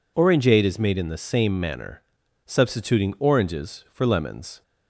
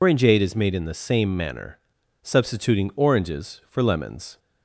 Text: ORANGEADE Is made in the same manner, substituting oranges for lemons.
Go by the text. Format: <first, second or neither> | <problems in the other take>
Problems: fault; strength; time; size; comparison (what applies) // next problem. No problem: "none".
first | loses the start of "ORANGEADE"; at 0.0 s; 90 ms